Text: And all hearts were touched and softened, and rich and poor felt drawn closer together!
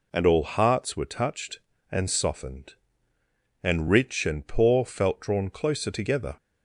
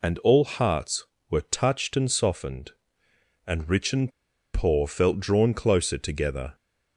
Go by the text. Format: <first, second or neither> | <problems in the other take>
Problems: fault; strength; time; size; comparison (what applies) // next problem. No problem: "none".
first | pauses between "and" and "poor"; at 4.1 s; 0.43 s long